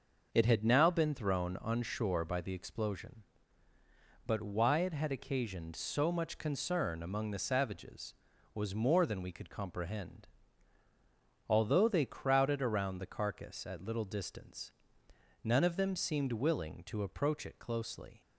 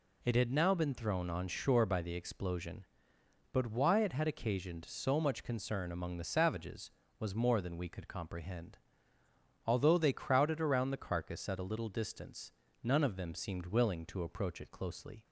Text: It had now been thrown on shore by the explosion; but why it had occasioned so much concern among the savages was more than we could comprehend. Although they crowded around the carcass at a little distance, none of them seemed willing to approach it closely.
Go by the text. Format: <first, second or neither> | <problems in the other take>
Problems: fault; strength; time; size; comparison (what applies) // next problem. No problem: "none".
second | skips "a"; at 13.8 s